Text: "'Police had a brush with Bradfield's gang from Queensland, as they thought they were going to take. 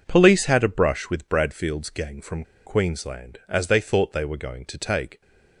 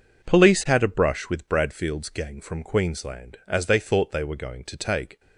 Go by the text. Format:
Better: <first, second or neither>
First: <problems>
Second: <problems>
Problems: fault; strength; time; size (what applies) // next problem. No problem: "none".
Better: second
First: pauses between "from" and "Queensland"; slight; at 2.4 s; 0.21 s long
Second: none